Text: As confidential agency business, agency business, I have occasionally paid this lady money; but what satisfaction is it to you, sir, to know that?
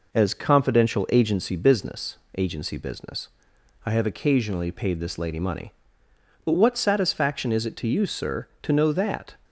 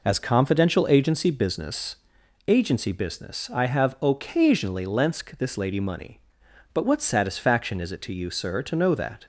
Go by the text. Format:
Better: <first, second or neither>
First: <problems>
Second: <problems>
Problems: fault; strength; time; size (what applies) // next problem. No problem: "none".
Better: first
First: none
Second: says "lensk" for "paid"; at 4.8 s